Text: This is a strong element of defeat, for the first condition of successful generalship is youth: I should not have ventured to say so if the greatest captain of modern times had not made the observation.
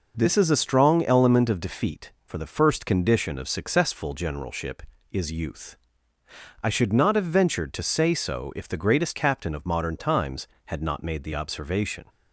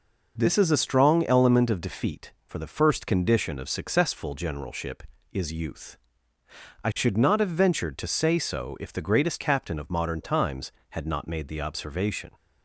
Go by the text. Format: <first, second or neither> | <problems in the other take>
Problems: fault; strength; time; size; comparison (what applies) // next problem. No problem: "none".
neither | none